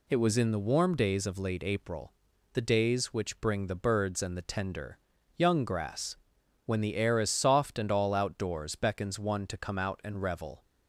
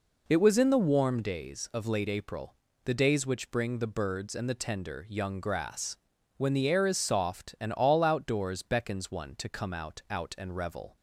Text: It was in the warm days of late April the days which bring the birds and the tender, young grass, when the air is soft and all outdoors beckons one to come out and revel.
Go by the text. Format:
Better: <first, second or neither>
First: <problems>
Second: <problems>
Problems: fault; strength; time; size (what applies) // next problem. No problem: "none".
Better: first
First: pauses between "April" and "the"; at 2.1 s; 0.40 s long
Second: pauses between "April" and "the"; slight; at 2.5 s; 0.30 s long // says "out" twice; at 10.0 s